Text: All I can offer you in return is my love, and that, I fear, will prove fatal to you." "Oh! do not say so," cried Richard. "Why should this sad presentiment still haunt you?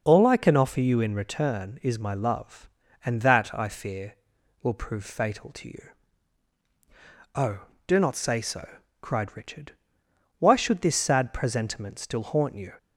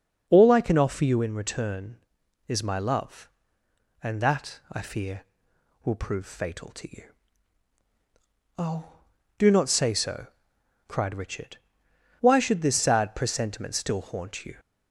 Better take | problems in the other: neither | none

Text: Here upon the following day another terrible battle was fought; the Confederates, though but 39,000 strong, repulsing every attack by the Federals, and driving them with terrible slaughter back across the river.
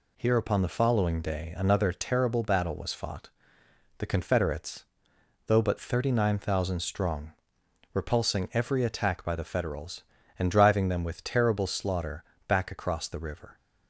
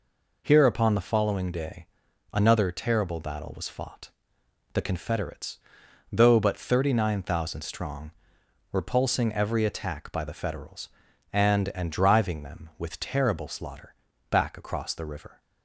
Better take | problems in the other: first | pauses between "day" and "another"; noticeable; at 1.8 s; 0.46 s long // says "and" twice; at 11.7 s // pauses between "slaughter" and "back"; slight; at 13.9 s; 0.36 s long; slight in the first

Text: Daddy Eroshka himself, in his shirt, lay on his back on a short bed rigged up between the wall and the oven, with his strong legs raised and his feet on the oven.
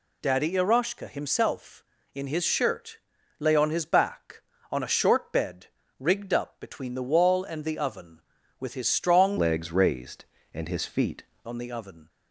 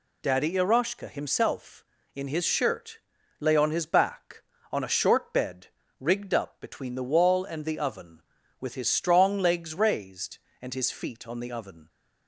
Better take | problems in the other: second | pauses between "bed" and "rigged"; slight; at 5.6 s; 0.32 s long; slight in the second // changes voice from "legs" to "feet"; from 9.3 to 11.2 s; 1.9 s long

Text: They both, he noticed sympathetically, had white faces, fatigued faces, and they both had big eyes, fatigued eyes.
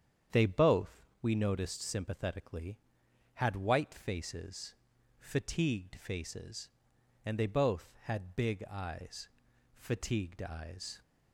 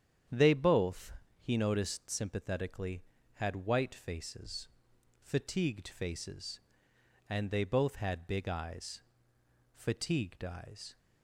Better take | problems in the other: second | starts louder than the rest; strong; until 1.4 s; 8.5 dB; strong in the second // says "we" for "he"; at 1.2 s

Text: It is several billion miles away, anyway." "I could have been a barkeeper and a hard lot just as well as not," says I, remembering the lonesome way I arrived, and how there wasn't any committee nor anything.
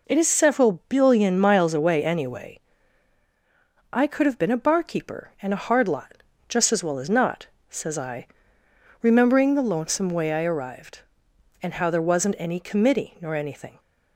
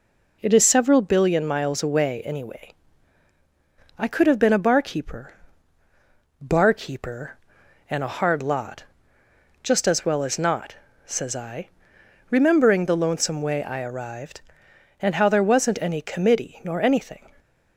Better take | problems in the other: first | says "barkeeper" twice; at 6.4 s // pauses between "lot" and "just"; noticeable; at 8.8 s; 0.80 s long; slight in the first

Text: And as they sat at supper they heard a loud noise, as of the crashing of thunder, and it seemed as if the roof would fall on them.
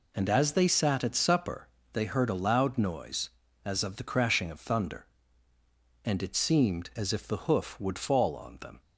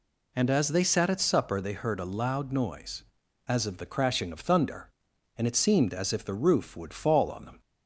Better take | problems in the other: second | pauses between "supper" and "they"; slight; at 1.6 s; 0.24 s long // says "hoof" for "roof"; at 7.4 s

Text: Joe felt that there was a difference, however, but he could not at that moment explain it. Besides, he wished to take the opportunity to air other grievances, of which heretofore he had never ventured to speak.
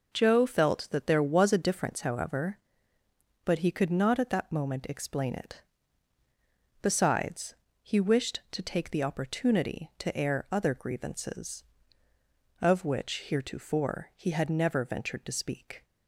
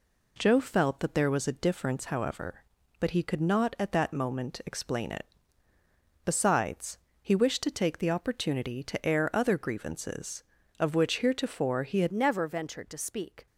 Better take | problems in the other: first | changes voice at "never"; from 12.1 s on; 1.3 s long

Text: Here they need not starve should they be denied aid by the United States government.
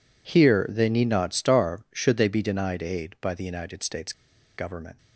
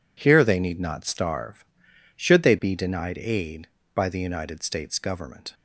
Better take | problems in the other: second | pauses between "States" and "government"; at 4.1 s; 0.44 s long

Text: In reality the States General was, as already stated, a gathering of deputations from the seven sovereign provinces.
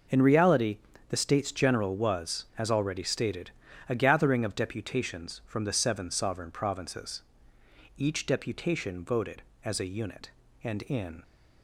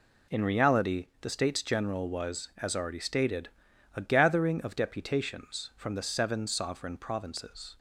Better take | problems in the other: second | pauses between "reality" and "the"; slight; at 0.7 s; 0.30 s long // goes on to say "Each deputation voted as a unit and in"; strong; from 7.9 s on; 3.2 s long

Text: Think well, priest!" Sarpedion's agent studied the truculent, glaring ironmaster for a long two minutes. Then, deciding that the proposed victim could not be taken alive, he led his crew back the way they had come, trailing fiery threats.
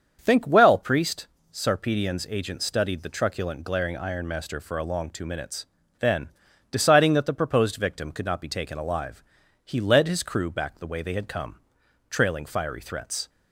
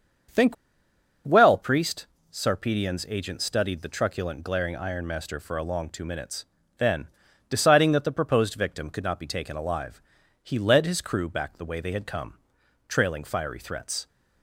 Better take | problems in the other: first | starts louder than the rest; until 2.0 s; 7 dB; also in the first // pauses between "Think" and "well"; noticeable; at 0.5 s; 0.70 s long

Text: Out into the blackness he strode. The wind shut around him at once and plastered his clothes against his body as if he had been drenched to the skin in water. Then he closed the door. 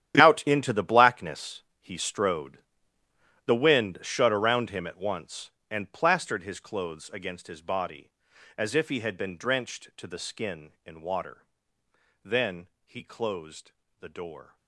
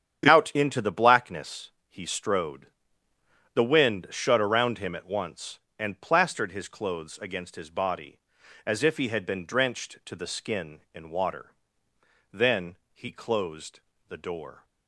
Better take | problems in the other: second | gets quieter; strong; throughout; 14.5 dB // starts louder than the rest; strong; until 1.2 s; 11 dB; strong in the second // pauses between "blackness" and "he"; slight; at 1.5 s; 0.22 s long; slight in the second // pauses between "Then" and "he"; slight; at 12.6 s; 0.18 s long; slight in the second // pauses between "closed" and "the"; slight; at 13.7 s; 0.28 s long; slight in the second

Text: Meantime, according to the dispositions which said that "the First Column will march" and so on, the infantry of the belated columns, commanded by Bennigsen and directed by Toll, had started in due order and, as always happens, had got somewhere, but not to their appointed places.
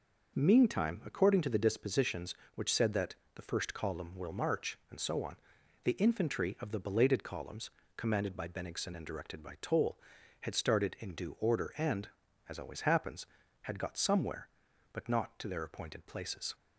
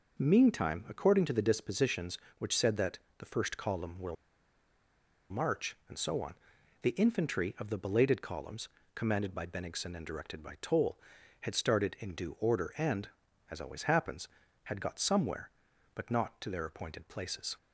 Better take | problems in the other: first | pauses between "that" and "the"; slight; at 2.9 s; 0.22 s long; slight in the first // pauses between "will" and "march"; at 4.1 s; 1.1 s long

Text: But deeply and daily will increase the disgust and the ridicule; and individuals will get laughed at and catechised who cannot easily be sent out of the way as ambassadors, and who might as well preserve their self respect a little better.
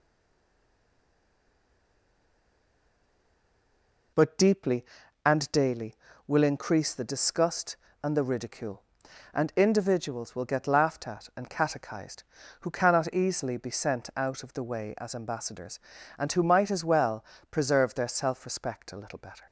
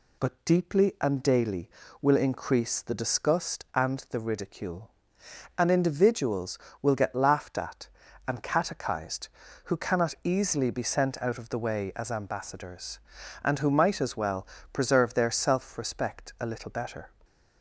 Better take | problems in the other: second | stays silent before the first word; strong; until 4.1 s; 4.1 s long // pauses between "well" and "preserve"; slight; at 17.2 s; 0.24 s long; slight in the second

